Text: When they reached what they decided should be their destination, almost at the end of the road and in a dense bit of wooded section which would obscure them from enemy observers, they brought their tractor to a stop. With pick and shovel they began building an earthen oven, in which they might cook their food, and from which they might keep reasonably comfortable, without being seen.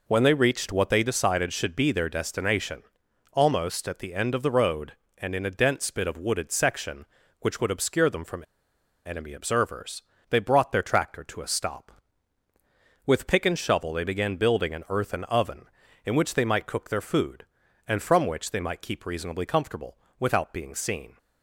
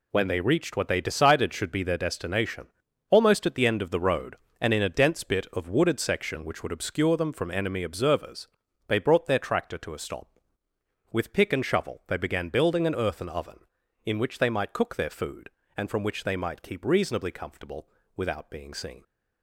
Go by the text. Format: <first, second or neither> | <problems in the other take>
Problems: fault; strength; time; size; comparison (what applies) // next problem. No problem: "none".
second | pauses between "from" and "enemy"; noticeable; at 8.4 s; 0.64 s long